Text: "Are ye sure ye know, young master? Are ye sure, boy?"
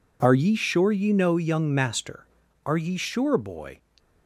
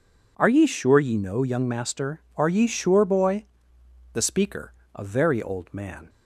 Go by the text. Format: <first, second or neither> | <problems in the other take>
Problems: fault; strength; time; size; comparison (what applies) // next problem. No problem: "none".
first | goes on to say "The speaker a very old man"; strong; from 4.1 s on; 1.9 s long